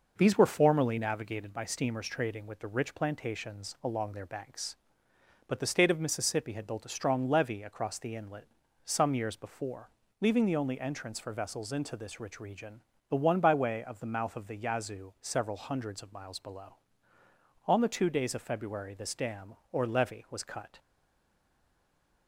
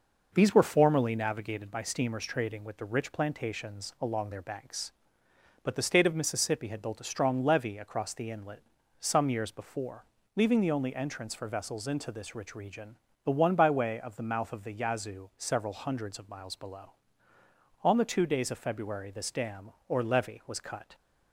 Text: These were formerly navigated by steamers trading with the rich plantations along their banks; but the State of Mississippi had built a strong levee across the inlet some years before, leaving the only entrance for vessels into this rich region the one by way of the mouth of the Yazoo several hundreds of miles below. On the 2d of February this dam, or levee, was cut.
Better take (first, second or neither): second